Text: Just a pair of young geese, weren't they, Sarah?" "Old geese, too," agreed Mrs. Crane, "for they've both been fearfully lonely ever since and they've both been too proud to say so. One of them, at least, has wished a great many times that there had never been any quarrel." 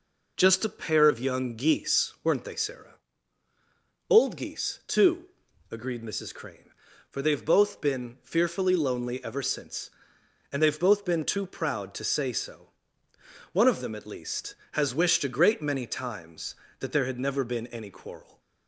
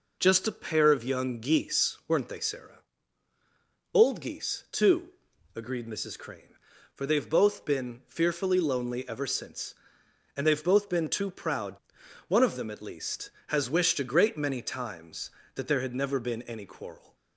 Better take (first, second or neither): first